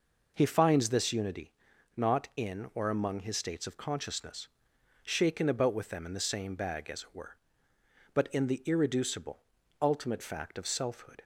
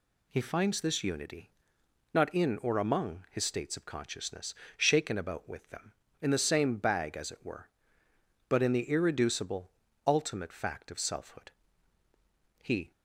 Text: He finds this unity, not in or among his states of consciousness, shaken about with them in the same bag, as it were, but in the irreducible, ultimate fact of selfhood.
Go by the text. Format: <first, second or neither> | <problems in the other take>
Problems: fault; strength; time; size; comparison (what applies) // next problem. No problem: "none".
first | goes on to say "He"; slight; from 12.6 s on; 0.30 s long